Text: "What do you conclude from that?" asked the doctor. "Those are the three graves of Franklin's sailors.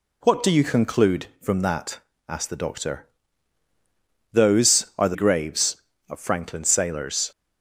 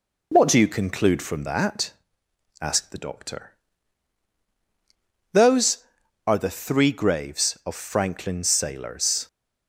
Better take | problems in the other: second | skips "three"; at 5.1 s

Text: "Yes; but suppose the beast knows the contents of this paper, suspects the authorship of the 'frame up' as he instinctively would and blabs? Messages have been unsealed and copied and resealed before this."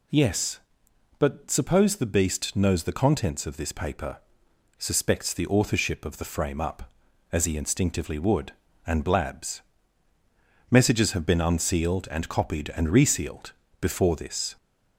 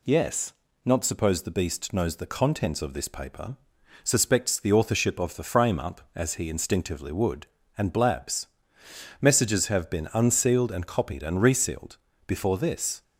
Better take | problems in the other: first | says "not" for "but"; at 0.8 s // pauses between "resealed" and "before"; slight; at 11.9 s; 0.28 s long; slight in the first

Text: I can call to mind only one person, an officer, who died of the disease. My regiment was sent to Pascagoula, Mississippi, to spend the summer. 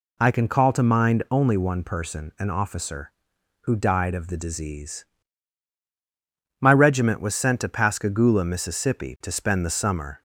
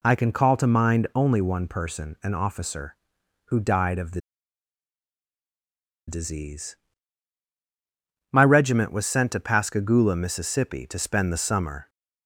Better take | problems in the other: first | pauses between "the" and "disease"; strong; at 4.2 s; 1.8 s long

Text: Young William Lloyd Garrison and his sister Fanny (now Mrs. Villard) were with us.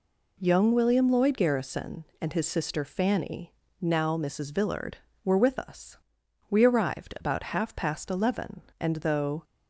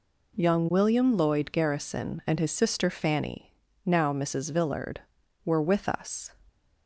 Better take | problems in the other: second | goes on to say "We arrived about half past eleven and though"; strong; from 6.4 s on; 2.9 s long

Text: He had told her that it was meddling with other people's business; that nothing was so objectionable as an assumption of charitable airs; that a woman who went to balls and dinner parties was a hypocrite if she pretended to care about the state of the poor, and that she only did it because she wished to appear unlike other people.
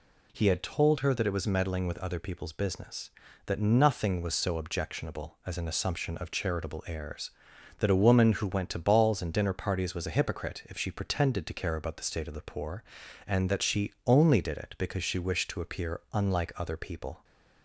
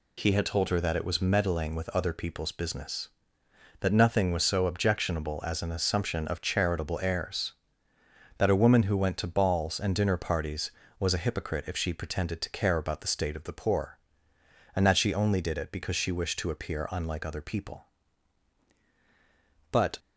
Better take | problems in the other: first | goes on to say "But"; slight; from 19.7 s on; 0.28 s long

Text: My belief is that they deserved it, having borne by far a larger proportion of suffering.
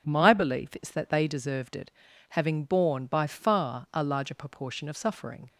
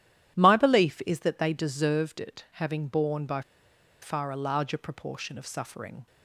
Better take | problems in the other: first | starts louder than the rest; strong; until 1.4 s; 11.5 dB // pauses between "by" and "far"; noticeable; at 3.4 s; 0.60 s long

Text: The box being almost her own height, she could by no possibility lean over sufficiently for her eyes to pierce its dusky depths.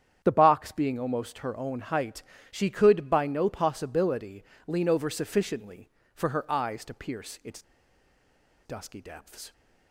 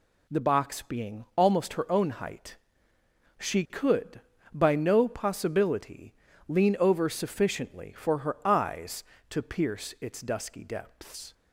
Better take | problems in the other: second | starts louder than the rest; strong; until 1.2 s; 9 dB // pauses between "possibility" and "lean"; slight; at 4.4 s; 0.24 s long; slight in the second // pauses between "its" and "dusky"; at 7.6 s; 1.0 s long

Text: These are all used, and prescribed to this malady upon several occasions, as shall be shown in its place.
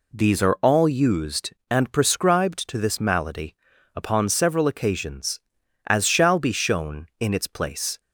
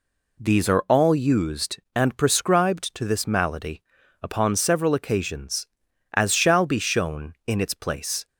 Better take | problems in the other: neither | pauses between "malady" and "upon"; the same in both

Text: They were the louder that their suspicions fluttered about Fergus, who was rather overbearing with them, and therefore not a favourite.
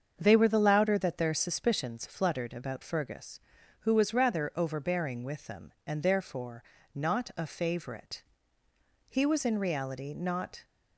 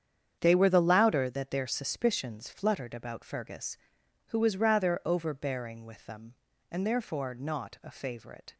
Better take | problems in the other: second | starts louder than the rest; until 1.2 s; 7 dB; strong in the second // pauses between "therefore" and "not"; slight; at 6.6 s; 0.32 s long // goes on to say "He was in reality not"; from 9.1 s on; 1.5 s long

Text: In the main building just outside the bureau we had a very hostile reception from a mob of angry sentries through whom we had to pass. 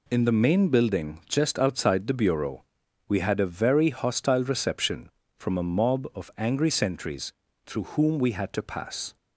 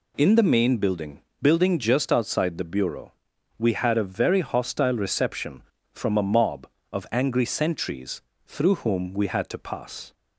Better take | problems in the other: first | says "building" twice; at 1.4 s // pauses between "bureau" and "we"; noticeable; at 3.1 s; 0.48 s long; noticeable in the first // pauses between "sentries" and "through"; slight; at 8.2 s; 0.26 s long; slight in the first

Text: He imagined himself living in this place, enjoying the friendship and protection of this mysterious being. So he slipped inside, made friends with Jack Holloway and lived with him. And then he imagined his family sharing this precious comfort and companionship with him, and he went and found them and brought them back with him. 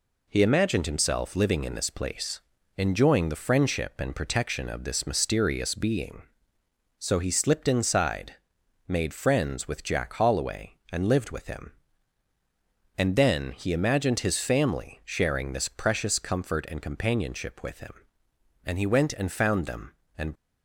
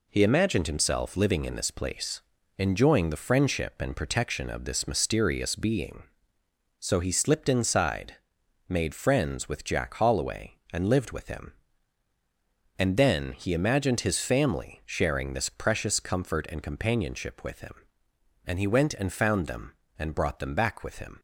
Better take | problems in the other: second | stops before "brought them back with him"; at 20.3 s

